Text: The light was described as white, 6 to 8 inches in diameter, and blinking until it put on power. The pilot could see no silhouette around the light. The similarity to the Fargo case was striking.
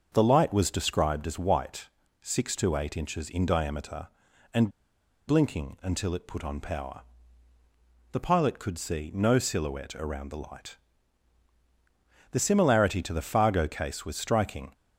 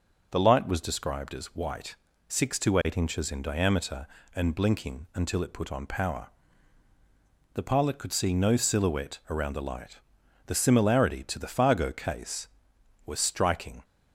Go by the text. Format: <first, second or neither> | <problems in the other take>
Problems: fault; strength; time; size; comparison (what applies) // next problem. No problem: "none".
second | starts louder than the rest; until 1.1 s; 6.5 dB // pauses between "and" and "blinking"; noticeable; at 4.6 s; 0.58 s long